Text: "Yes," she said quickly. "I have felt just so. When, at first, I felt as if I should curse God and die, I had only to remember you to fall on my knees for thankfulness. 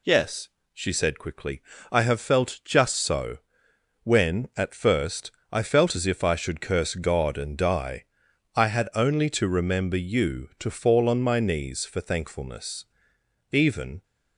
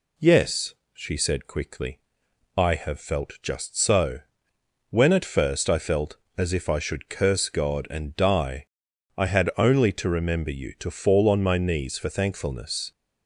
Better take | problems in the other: second | goes on to say "Even"; from 13.5 s on; 0.52 s long

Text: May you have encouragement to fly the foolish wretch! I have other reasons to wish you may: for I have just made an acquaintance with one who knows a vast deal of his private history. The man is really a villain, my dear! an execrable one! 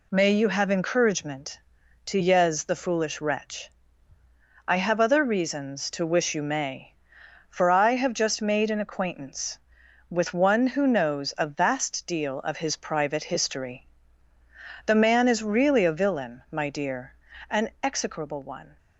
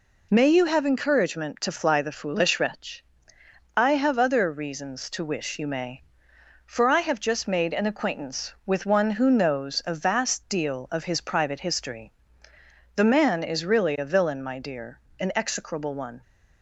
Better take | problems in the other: second | says "yez" for "fly"; at 2.2 s

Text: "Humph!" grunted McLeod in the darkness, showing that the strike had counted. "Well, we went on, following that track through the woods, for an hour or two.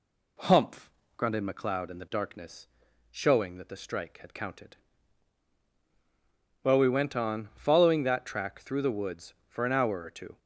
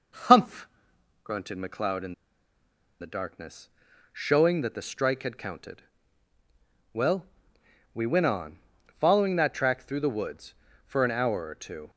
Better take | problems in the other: first | pauses between "in" and "the"; noticeable; at 2.1 s; 0.88 s long

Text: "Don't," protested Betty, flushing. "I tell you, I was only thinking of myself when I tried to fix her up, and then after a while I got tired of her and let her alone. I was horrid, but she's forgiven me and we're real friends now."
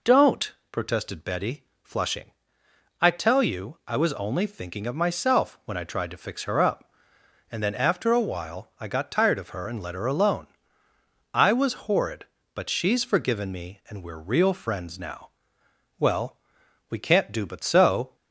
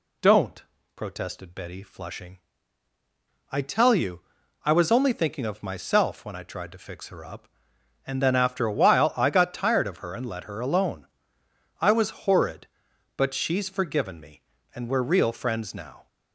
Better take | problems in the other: second | goes on to say "Well we can't do but so"; strong; from 15.9 s on; 2.1 s long

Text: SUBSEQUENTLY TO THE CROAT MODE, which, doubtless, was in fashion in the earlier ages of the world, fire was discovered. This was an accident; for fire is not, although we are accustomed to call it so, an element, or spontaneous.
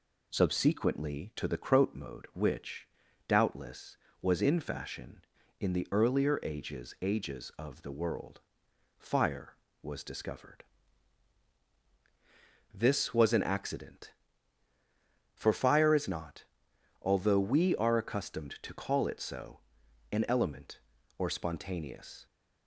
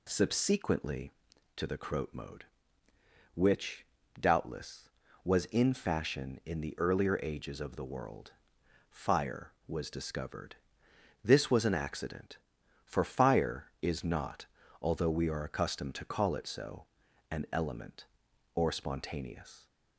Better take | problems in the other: second | says "ages" twice; at 7.0 s

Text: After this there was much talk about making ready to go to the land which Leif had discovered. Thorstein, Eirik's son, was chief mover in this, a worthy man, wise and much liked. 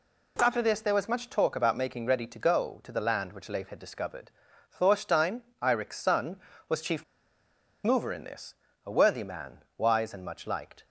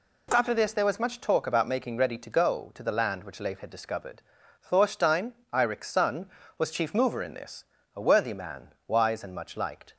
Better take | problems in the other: second | pauses between "chief" and "mover"; noticeable; at 7.0 s; 0.80 s long

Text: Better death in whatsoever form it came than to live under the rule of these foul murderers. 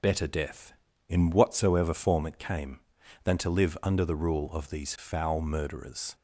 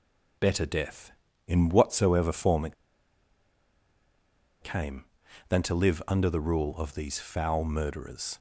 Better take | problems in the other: first | pauses between "it" and "came"; strong; at 2.7 s; 1.8 s long

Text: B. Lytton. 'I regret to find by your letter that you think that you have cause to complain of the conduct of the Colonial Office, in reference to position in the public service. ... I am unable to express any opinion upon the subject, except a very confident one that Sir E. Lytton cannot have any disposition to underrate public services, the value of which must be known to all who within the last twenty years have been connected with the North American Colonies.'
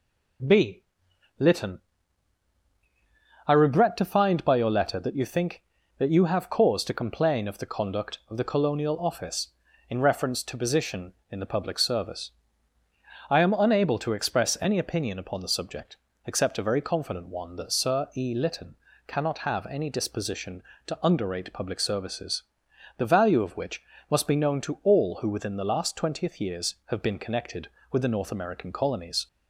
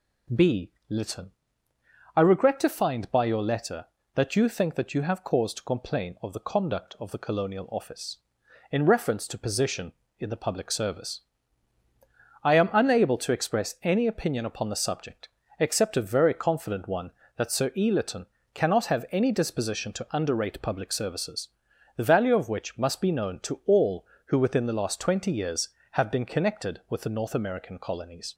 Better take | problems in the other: second | pauses between "Lytton" and "cannot"; slight; at 18.7 s; 0.28 s long; slight in the second // pauses between "which" and "must"; slight; at 23.8 s; 0.26 s long // says "twentieth" for "twenty"; at 25.9 s

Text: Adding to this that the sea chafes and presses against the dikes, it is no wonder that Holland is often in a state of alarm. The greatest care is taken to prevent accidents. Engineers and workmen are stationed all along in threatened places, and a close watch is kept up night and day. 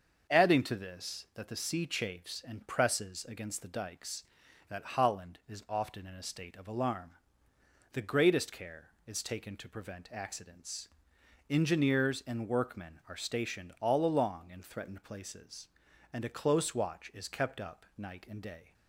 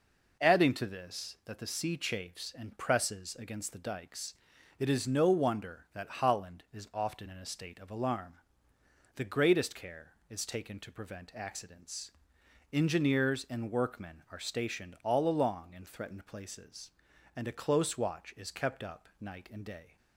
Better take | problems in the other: second | starts louder than the rest; until 1.4 s; 6.5 dB // skips "it is no wonder"; at 4.4 s

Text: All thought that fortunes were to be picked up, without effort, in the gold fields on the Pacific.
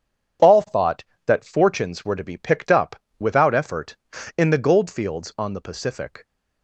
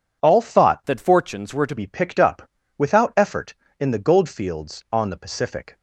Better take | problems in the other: first | changes voice from "that" to "to"; from 0.8 to 1.7 s; 0.9 s long

